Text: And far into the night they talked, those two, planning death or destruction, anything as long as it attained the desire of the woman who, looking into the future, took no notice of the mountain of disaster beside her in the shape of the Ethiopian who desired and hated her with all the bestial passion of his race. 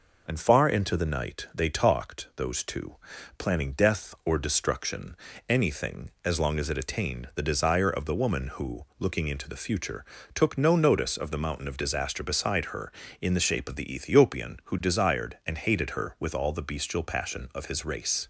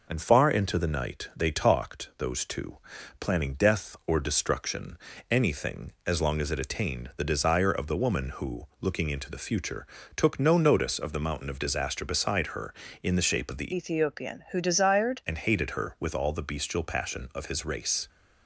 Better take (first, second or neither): first